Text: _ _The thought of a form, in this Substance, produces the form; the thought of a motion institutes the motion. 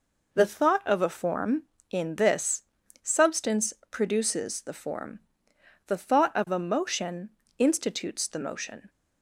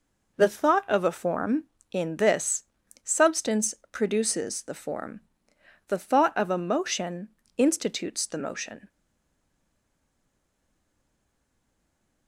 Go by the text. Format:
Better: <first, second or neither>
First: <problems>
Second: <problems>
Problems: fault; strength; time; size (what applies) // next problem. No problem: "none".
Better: first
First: pauses between "this" and "Substance"; at 2.6 s; 0.40 s long // pauses between "motion" and "institutes"; slight; at 7.2 s; 0.30 s long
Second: pauses between "this" and "Substance"; at 2.6 s; 0.40 s long // pauses between "motion" and "institutes"; slight; at 7.2 s; 0.30 s long // stays silent after the last word; strong; from 8.8 s on; 3.4 s long